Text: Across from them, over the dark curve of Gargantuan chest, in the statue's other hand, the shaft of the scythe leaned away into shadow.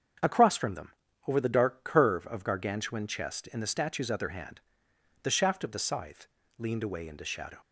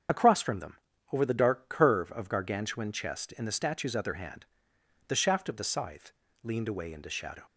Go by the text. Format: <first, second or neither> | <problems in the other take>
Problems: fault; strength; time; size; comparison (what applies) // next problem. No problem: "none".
first | loses the start of "Across"; at 0.0 s; 70 ms // starts louder than the rest; strong; until 1.4 s; 7.5 dB; strong in the first // pauses between "scythe" and "leaned"; slight; at 6.1 s; 0.32 s long; slight in the first